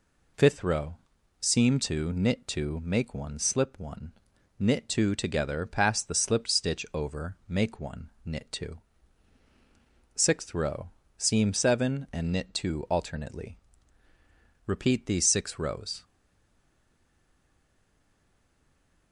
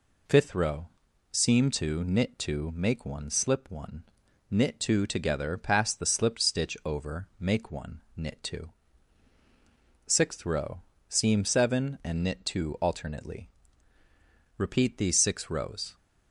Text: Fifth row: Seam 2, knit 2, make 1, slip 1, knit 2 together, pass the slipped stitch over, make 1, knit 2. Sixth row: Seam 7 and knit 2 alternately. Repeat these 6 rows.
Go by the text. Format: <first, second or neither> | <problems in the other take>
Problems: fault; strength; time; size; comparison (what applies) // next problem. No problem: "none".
second | stays silent after the last word; strong; from 16.0 s on; 3.1 s long